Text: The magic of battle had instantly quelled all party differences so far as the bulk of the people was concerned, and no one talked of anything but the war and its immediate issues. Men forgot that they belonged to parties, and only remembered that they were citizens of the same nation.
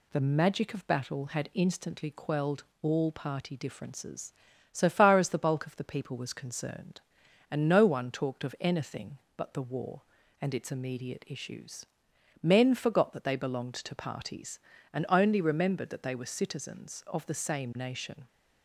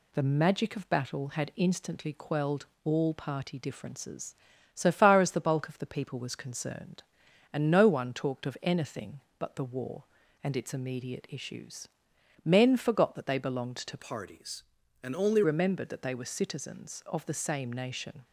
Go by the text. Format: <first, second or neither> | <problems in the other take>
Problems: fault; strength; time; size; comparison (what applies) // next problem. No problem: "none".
first | pauses between "quelled" and "all"; slight; at 2.6 s; 0.18 s long; slight in the first // changes voice from "parties" to "only"; from 13.9 to 15.4 s; 1.5 s long